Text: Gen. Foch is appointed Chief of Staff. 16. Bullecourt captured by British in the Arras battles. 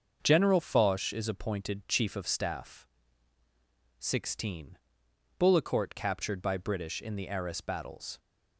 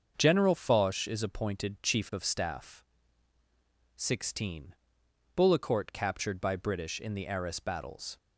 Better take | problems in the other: neither | starts louder than the rest; the same in both

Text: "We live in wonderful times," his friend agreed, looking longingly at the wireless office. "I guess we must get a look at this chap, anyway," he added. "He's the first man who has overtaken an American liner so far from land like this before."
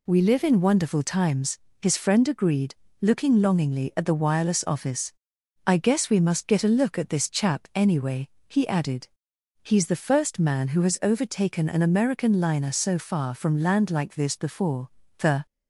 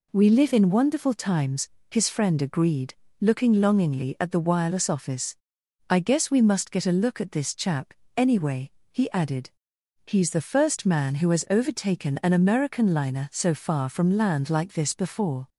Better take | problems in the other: second | goes on to say "The"; slight; from 15.1 s on; 0.26 s long

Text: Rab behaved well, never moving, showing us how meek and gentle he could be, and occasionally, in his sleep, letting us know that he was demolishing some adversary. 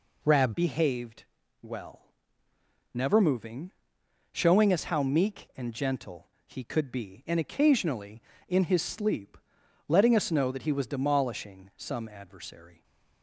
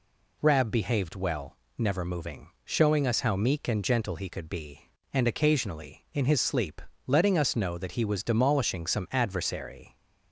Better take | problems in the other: second | changes voice at "behaved"; from 0.5 s on; 12.3 s long // pauses between "behaved" and "well"; at 1.2 s; 0.38 s long // pauses between "gentle" and "he"; slight; at 6.2 s; 0.18 s long

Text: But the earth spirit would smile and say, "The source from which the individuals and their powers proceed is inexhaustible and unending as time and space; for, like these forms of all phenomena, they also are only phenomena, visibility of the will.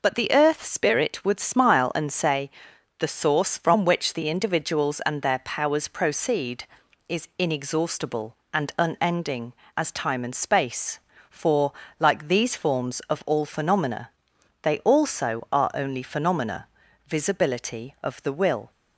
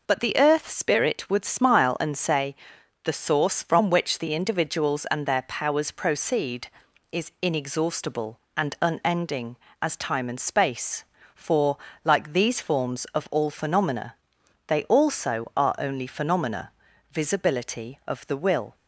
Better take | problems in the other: neither | none

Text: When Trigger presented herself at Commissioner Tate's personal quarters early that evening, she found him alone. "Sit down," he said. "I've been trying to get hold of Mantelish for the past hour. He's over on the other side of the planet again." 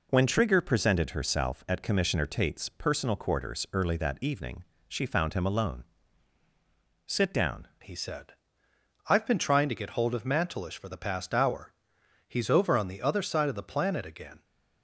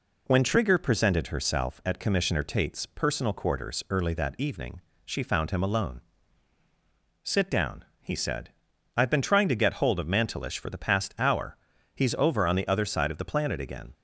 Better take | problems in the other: second | changes voice at "he"; from 7.8 s on; 6.6 s long

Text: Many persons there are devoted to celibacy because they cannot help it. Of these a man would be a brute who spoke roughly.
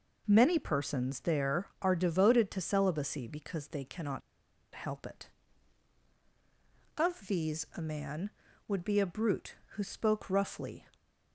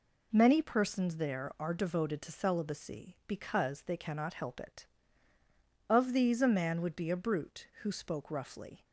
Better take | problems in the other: second | pauses between "cannot" and "help"; noticeable; at 4.2 s; 0.54 s long

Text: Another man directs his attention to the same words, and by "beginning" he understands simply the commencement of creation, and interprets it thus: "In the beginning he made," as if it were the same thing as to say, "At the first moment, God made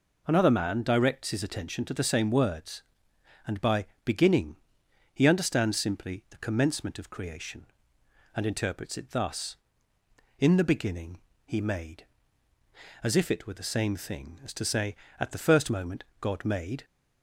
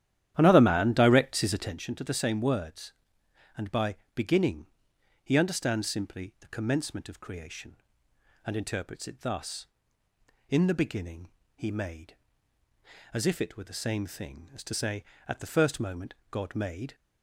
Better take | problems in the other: first | starts louder than the rest; strong; until 1.8 s; 11.5 dB // pauses between "by" and "beginning"; slight; at 3.9 s; 0.22 s long; slight in the first // pauses between "beginning" and "he"; noticeable; at 4.6 s; 0.56 s long; noticeable in the first // pauses between "beginning" and "he"; slight; at 11.3 s; 0.24 s long; slight in the first

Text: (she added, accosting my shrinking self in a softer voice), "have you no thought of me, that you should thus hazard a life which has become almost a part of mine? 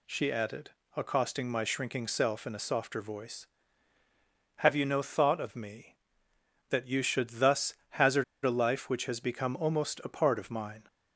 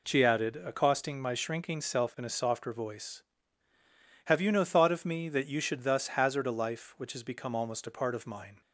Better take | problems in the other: second | pauses between "thus" and "hazard"; slight; at 7.7 s; 0.18 s long // pauses between "hazard" and "a"; slight; at 8.2 s; 0.20 s long

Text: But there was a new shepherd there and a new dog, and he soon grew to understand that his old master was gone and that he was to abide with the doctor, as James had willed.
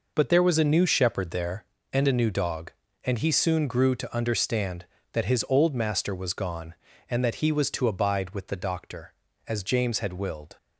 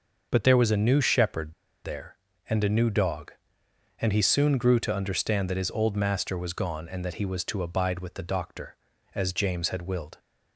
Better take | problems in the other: first | pauses between "shepherd" and "there"; slight; at 1.5 s; 0.31 s long

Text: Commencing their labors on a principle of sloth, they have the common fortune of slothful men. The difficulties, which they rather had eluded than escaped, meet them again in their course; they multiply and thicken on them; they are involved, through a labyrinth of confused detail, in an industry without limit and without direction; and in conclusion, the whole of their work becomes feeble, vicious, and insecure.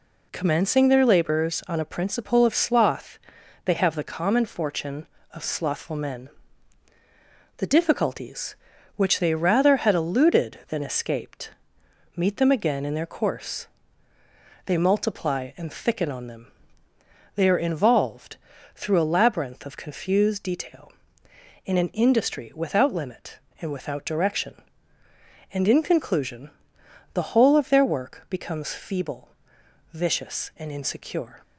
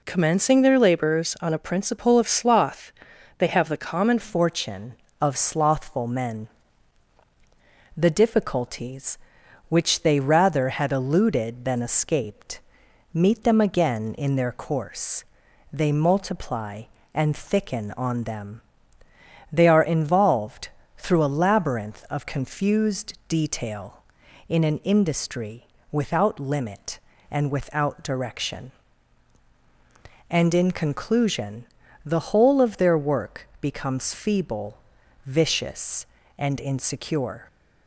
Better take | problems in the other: first | changes voice at "fortune"; from 4.2 s on; 33.2 s long // pauses between "confused" and "detail"; slight; at 23.1 s; 0.16 s long // pauses between "industry" and "without"; slight; at 25.6 s; 0.24 s long

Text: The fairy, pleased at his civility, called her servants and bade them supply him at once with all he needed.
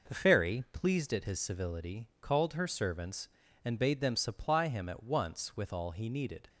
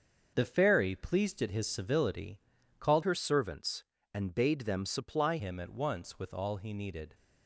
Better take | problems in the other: first | starts louder than the rest; until 1.3 s; 6.5 dB // changes voice from "her" to "supply"; from 3.0 to 5.3 s; 2.3 s long

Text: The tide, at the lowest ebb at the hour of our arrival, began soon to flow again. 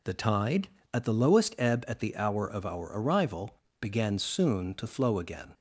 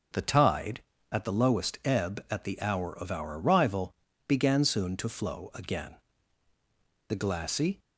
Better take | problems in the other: first | goes on to say "The glassy"; noticeable; from 7.0 s on; 0.70 s long

